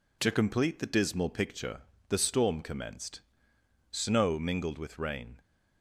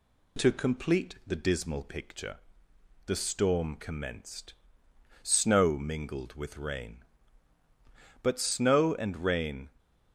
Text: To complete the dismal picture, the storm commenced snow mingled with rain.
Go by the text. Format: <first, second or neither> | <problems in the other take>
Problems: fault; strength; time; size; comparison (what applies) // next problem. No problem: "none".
first | pauses between "commenced" and "snow"; noticeable; at 4.5 s; 0.70 s long; noticeable in the first // goes on to say "But snow and rain"; from 8.2 s on; 1.4 s long